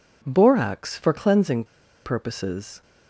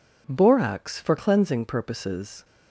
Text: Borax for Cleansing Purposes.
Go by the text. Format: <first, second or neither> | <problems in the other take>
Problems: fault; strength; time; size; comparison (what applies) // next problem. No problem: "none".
second | pauses between "Cleansing" and "Purposes"; at 1.6 s; 0.40 s long